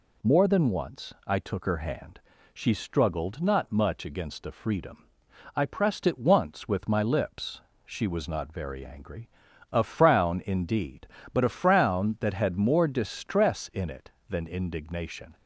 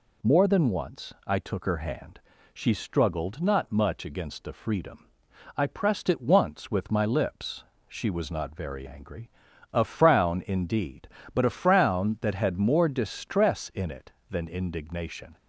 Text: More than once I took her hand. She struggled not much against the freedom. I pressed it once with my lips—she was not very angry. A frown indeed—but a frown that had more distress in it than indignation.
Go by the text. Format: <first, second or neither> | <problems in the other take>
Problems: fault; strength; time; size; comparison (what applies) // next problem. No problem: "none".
neither | none